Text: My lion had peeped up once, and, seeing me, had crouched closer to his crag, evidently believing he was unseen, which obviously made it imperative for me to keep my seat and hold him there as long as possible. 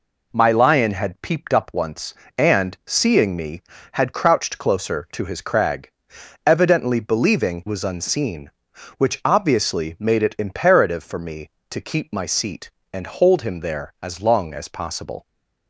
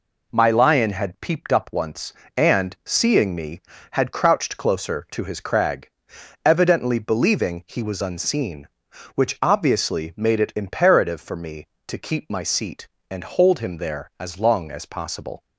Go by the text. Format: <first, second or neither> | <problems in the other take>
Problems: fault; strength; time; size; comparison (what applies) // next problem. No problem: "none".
second | skips "he"; at 7.6 s